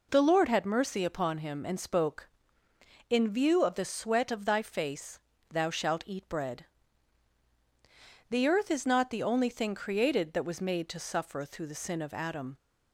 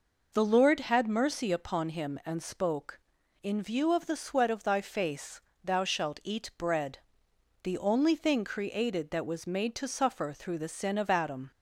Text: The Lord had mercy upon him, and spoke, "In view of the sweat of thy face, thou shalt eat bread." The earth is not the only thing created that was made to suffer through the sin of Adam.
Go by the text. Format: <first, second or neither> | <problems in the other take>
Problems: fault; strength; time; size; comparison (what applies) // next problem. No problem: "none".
first | skips "The earth is not"; at 7.3 s